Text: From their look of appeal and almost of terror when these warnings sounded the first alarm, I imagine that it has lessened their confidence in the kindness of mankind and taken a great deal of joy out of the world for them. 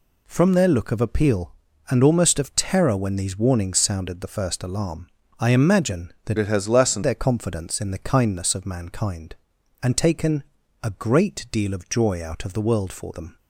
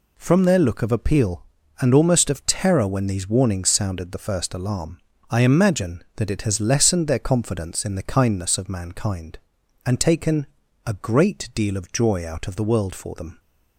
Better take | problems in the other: second | changes voice from "it" to "lessened"; from 6.3 to 7.0 s; 0.7 s long // pauses between "taken" and "a"; at 10.4 s; 0.40 s long; also in the second

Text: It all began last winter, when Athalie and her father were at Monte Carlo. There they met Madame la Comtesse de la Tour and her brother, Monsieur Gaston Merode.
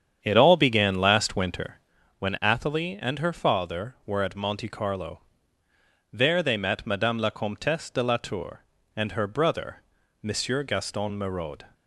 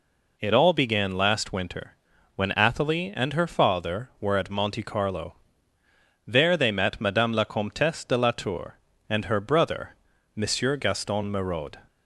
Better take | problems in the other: second | starts louder than the rest; strong; until 1.9 s; 8.5 dB

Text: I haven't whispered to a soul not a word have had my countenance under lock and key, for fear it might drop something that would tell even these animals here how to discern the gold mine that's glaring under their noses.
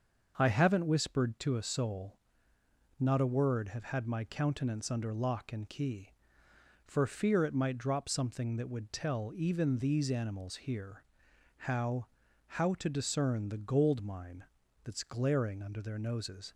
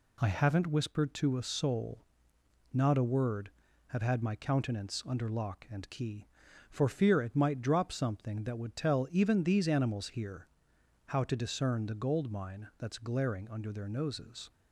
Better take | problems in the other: second | starts louder than the rest; until 1.3 s; 6.5 dB // pauses between "soul" and "not"; noticeable; at 2.1 s; 0.82 s long; noticeable in the second // pauses between "here" and "how"; noticeable; at 11.0 s; 0.54 s long; noticeable in the second // says "how" twice; at 12.4 s // pauses between "mine" and "that's"; at 14.4 s; 0.40 s long

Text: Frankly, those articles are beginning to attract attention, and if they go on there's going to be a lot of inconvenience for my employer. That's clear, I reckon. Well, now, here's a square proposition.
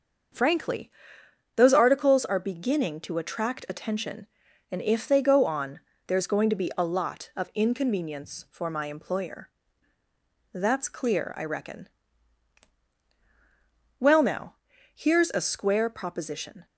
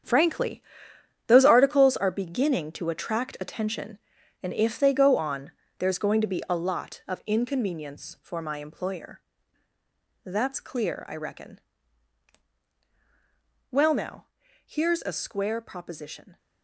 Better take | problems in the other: first | gets quieter; strong; throughout; 11.5 dB // starts louder than the rest; strong; until 1.7 s; 8.5 dB; also in the first // pauses between "on" and "there's"; slight; at 5.5 s; 0.28 s long; slight in the first

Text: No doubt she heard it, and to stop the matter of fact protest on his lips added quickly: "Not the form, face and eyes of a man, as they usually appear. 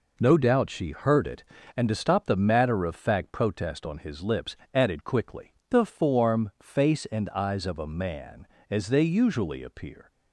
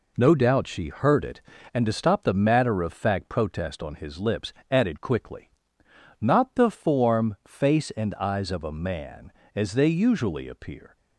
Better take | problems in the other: second | pauses between "lips" and "added"; slight; at 4.5 s; 0.16 s long; slight in the second // skips "Not"; at 5.6 s

